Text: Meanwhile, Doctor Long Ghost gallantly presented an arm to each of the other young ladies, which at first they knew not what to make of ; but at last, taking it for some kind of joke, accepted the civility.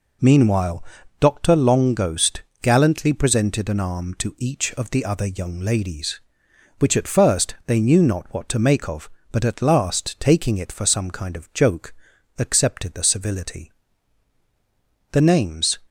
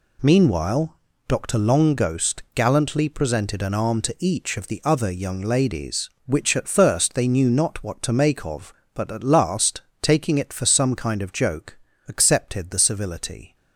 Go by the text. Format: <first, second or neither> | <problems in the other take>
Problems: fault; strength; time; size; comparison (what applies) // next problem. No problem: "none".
second | pauses between "Ghost" and "gallantly"; slight; at 2.4 s; 0.22 s long // goes on to say "The names"; noticeable; from 15.1 s on; 0.68 s long